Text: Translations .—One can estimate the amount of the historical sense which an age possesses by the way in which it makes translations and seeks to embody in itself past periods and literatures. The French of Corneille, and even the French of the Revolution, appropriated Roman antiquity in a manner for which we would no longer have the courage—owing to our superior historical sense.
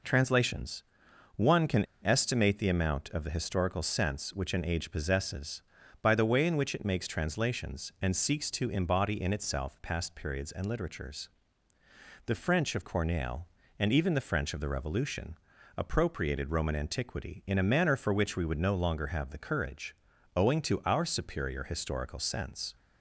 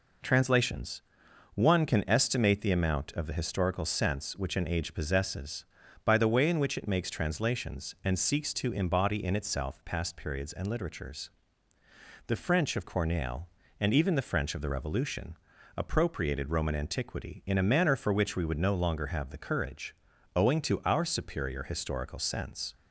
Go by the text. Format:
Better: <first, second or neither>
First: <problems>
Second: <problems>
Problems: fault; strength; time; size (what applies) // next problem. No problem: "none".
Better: second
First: pauses between "can" and "estimate"; slight; at 1.8 s; 0.18 s long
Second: none